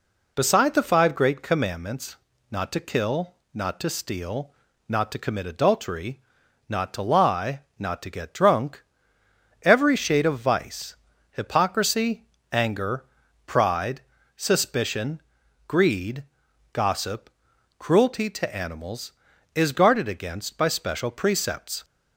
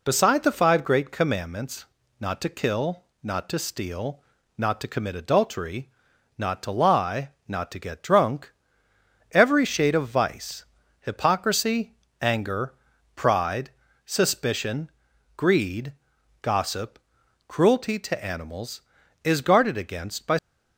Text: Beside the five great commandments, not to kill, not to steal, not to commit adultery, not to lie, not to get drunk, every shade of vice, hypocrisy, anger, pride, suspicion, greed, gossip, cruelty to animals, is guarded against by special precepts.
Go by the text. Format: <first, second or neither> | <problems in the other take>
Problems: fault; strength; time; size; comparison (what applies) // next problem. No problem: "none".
first | stops before "special precepts"; at 20.3 s